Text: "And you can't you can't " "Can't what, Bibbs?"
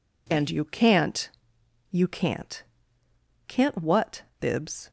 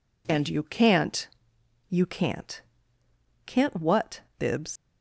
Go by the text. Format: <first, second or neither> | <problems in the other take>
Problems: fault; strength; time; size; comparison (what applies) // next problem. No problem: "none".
first | pauses between "can't" and "you"; noticeable; at 1.2 s; 0.60 s long; noticeable in the first // leaves "Bibbs" unfinished; at 4.7 s; 120 ms